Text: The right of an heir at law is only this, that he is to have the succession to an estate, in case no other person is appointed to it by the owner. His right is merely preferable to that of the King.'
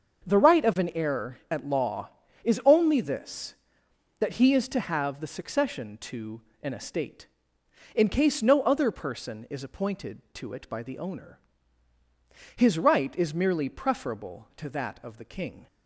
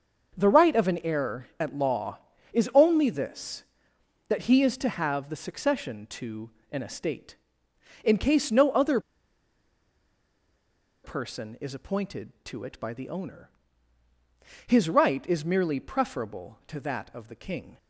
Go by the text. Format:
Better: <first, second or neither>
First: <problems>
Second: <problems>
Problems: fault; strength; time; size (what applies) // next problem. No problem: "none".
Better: first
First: starts louder than the rest; until 1.3 s; 7 dB // pauses between "to" and "an"; slight; at 6.4 s; 0.22 s long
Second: starts louder than the rest; until 1.4 s; 6.5 dB // pauses between "to" and "an"; slight; at 6.4 s; 0.22 s long // pauses between "other" and "person"; strong; at 8.9 s; 2.0 s long